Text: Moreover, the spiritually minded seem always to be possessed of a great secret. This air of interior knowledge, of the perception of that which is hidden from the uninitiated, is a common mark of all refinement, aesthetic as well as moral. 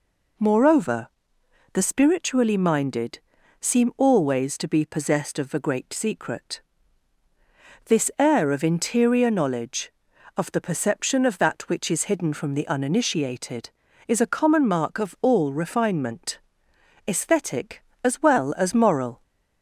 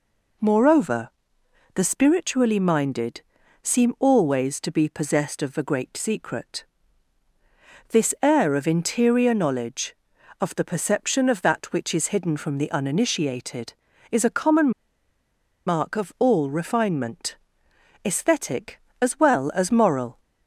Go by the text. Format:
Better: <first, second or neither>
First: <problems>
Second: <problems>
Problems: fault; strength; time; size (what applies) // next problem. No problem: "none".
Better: first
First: pauses between "minded" and "seem"; at 3.1 s; 0.40 s long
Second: pauses between "minded" and "seem"; at 3.2 s; 0.40 s long // pauses between "common" and "mark"; noticeable; at 14.6 s; 0.96 s long